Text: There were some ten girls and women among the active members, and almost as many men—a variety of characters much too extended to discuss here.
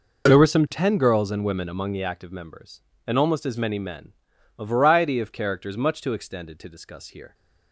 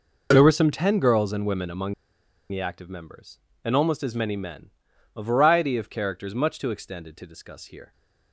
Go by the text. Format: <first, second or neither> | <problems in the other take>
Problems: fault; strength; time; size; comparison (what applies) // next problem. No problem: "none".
first | pauses between "among" and "the"; noticeable; at 1.9 s; 0.58 s long